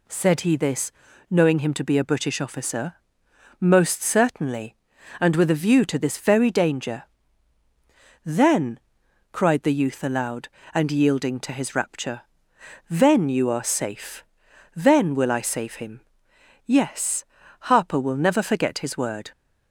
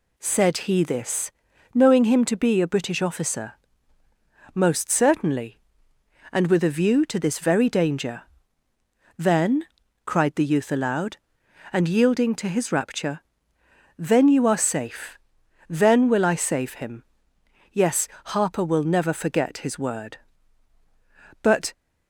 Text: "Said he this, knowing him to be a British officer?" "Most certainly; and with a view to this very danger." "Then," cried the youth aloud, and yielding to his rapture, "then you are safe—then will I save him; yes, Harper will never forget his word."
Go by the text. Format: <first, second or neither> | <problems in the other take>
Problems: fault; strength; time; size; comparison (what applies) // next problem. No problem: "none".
first | goes on to say "But"; slight; from 21.4 s on; 0.30 s long